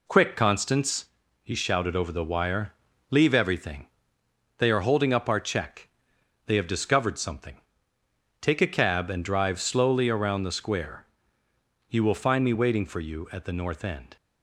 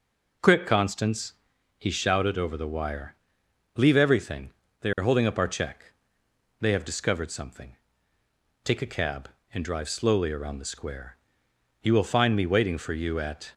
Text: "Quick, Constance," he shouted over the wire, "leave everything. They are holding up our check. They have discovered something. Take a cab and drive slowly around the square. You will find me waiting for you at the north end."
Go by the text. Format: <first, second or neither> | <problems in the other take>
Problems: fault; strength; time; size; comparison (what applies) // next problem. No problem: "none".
first | stops before "the north end"; at 13.5 s